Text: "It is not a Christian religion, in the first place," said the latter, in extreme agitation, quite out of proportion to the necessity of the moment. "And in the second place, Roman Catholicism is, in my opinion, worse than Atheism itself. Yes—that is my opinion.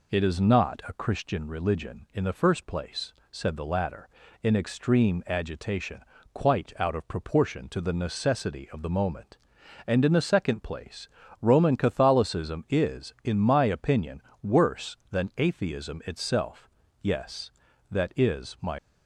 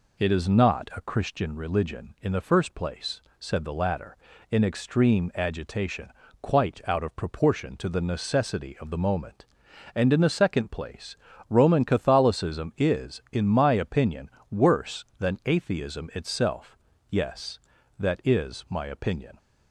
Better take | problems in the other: second | stops before "opinion"; at 18.7 s

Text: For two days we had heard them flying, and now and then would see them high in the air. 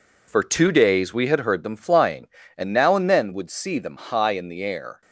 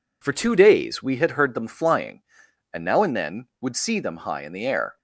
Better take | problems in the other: neither | none

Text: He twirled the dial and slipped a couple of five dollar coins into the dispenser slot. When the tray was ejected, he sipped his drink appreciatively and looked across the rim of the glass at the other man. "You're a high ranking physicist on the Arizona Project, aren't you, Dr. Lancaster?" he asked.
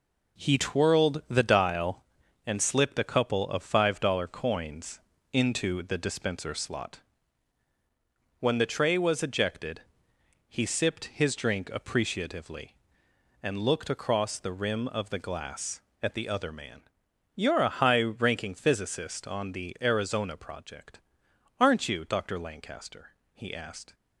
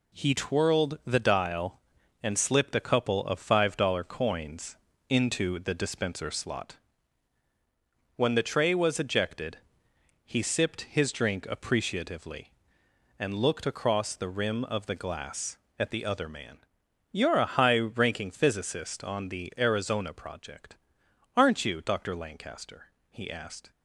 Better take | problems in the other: second | starts louder than the rest; noticeable; until 2.1 s; 4.5 dB // pauses between "coins" and "into"; slight; at 5.0 s; 0.32 s long; slight in the second

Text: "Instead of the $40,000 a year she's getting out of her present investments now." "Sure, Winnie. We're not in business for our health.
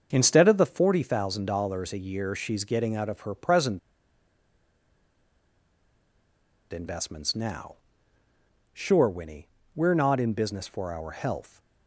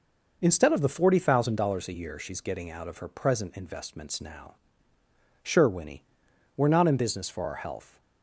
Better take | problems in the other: second | starts louder than the rest; until 1.1 s; 6.5 dB // pauses between "present" and "investments"; strong; at 3.7 s; 2.9 s long

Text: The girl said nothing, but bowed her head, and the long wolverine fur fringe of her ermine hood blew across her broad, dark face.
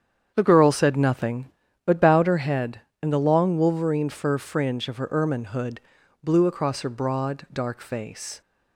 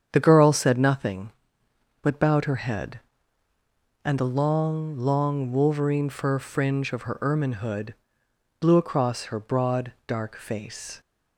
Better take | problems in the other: first | starts louder than the rest; strong; until 1.1 s; 8 dB; strong in the first // says "long" twice; at 4.9 s // pauses between "hood" and "blew"; noticeable; at 7.9 s; 0.64 s long; also in the first

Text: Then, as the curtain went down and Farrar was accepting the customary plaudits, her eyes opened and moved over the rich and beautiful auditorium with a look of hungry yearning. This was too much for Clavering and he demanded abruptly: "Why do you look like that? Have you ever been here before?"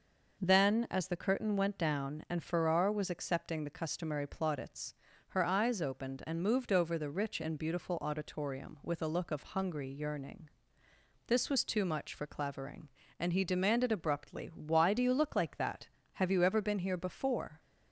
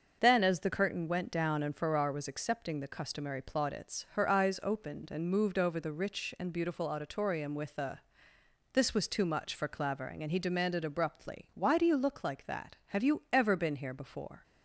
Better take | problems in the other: first | starts louder than the rest; until 1.2 s; 6.5 dB // skips "look of hungry yearning"; at 8.3 s

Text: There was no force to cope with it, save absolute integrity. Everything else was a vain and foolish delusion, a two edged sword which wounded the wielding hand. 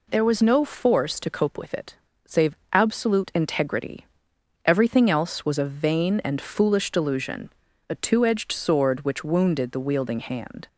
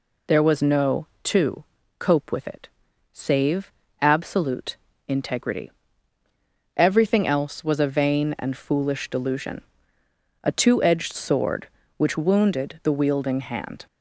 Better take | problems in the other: first | skips "force"; at 1.1 s // pauses between "to" and "cope"; slight; at 1.6 s; 0.34 s long // pauses between "save" and "absolute"; slight; at 3.7 s; 0.28 s long; slight in the first // pauses between "absolute" and "integrity"; slight; at 4.7 s; 0.32 s long

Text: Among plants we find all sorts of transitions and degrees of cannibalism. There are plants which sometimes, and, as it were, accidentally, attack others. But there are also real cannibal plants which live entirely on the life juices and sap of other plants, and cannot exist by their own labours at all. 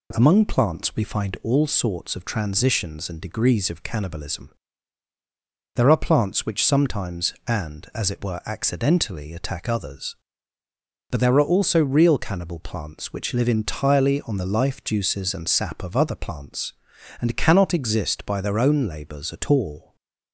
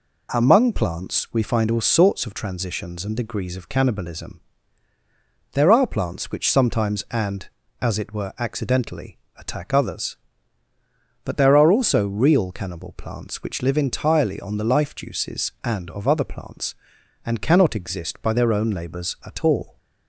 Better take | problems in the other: first | skips "sap"; at 15.9 s

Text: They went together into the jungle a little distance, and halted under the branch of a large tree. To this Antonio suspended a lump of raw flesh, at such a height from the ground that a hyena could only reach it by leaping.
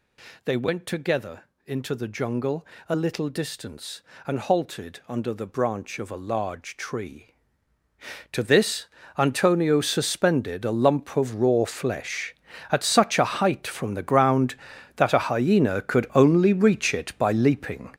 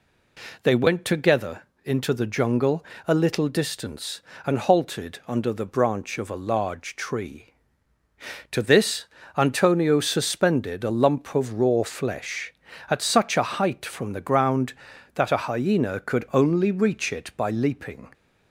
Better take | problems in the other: second | gets louder; strong; throughout; 9.5 dB // pauses between "together" and "into"; slight; at 1.4 s; 0.22 s long; slight in the second // pauses between "jungle" and "a"; slight; at 2.6 s; 0.22 s long; slight in the second // pauses between "this" and "Antonio"; slight; at 8.8 s; 0.30 s long; slight in the second

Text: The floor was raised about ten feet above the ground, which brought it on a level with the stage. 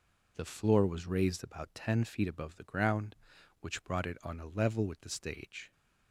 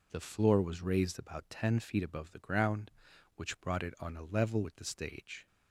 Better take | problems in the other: neither | none

